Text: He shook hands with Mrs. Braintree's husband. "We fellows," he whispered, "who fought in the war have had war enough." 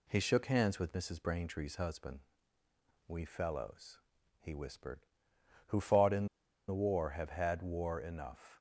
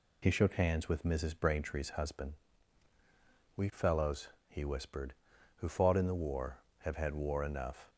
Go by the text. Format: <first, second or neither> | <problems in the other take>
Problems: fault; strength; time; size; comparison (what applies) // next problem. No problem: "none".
second | pauses between "in" and "the"; at 6.2 s; 0.42 s long